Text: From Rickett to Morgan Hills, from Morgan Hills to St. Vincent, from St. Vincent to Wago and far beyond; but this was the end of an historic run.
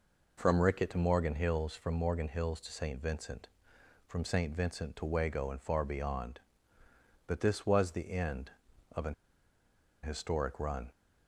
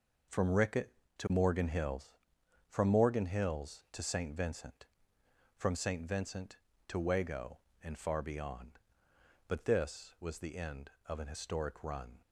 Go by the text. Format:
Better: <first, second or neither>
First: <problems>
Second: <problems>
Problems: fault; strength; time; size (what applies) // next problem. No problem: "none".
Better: second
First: pauses between "an" and "historic"; noticeable; at 9.1 s; 0.88 s long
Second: none